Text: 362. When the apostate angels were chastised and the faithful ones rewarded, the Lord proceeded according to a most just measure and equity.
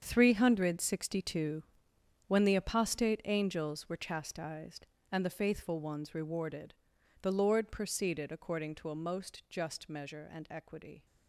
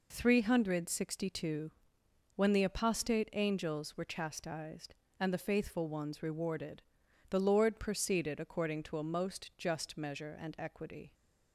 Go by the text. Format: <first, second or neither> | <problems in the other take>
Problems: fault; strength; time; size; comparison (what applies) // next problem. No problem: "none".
second | gets quieter; strong; throughout; 12 dB